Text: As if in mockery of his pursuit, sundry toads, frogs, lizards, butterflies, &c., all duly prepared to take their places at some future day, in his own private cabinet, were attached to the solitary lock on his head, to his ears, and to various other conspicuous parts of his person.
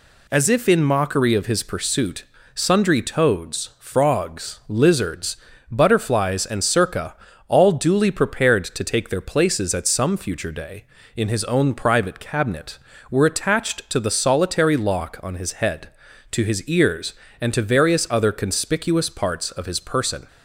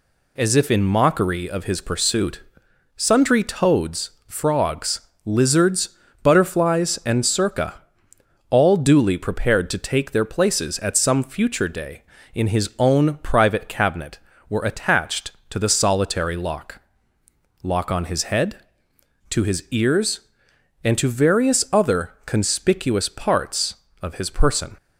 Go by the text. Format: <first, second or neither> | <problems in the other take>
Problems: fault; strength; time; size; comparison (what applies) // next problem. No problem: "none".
first | says "lock" twice; at 17.6 s